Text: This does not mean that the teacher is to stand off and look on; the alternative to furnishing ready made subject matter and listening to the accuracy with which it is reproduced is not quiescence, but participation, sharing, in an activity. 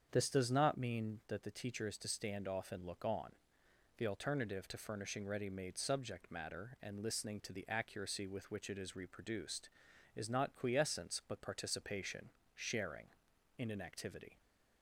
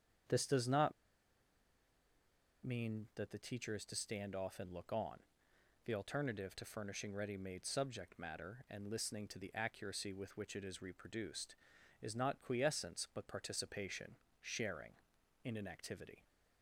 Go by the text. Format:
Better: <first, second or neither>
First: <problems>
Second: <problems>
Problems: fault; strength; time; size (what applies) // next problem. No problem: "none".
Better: first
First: starts louder than the rest; strong; until 1.1 s; 7.5 dB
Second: starts louder than the rest; strong; until 3.0 s; 7.5 dB // pauses between "not" and "mean"; strong; at 0.9 s; 1.7 s long